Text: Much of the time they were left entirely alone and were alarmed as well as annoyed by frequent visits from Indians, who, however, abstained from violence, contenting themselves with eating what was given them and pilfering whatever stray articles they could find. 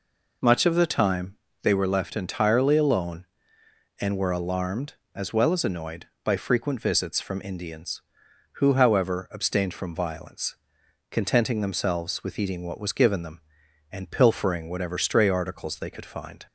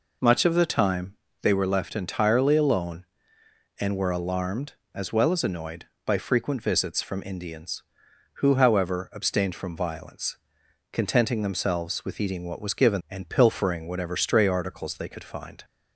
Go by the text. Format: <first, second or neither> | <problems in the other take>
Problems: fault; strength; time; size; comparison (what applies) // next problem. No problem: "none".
first | pauses between "time" and "they"; slight; at 1.1 s; 0.28 s long; slight in the first // skips "them"; at 13.0 s